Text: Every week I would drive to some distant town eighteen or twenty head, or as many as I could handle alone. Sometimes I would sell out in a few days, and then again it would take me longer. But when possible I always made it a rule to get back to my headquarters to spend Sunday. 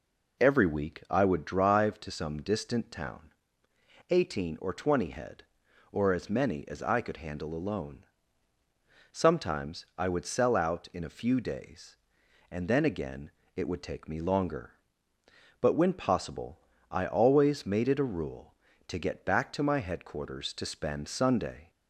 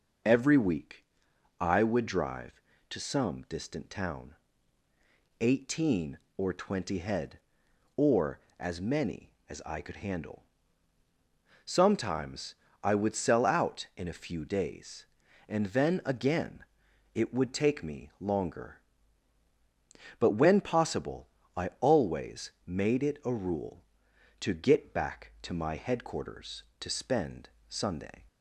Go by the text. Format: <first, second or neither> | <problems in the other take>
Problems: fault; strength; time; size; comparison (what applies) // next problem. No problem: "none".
first | pauses between "week" and "I"; noticeable; at 1.0 s; 0.56 s long // pauses between "town" and "eighteen"; at 4.3 s; 1.0 s long; noticeable in the first // skips "alone"; at 11.0 s // pauses between "Sometimes" and "I"; slight; at 12.5 s; 0.30 s long // pauses between "again" and "it"; noticeable; at 16.6 s; 0.50 s long; slight in the first // pauses between "possible" and "I"; slight; at 21.2 s; 0.28 s long; slight in the first // pauses between "always" and "made"; slight; at 22.5 s; 0.16 s long // pauses between "spend" and "Sunday"; slight; at 27.4 s; 0.20 s long